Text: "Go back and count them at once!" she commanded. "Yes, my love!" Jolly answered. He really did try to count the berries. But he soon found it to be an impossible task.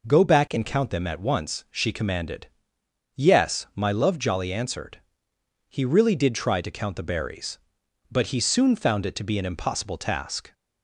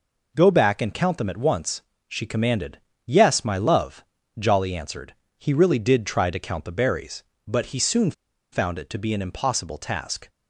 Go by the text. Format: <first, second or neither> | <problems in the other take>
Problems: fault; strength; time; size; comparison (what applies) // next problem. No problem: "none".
first | pauses between "soon" and "found"; at 8.1 s; 0.40 s long